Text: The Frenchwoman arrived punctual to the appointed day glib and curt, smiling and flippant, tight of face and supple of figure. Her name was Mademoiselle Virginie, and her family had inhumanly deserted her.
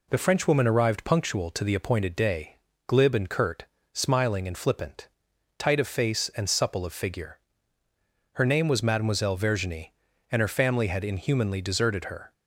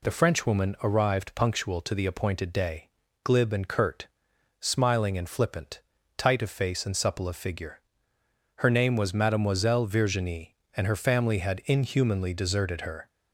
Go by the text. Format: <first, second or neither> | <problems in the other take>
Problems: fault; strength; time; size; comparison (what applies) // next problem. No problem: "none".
neither | pauses between "day" and "glib"; slight; the same in both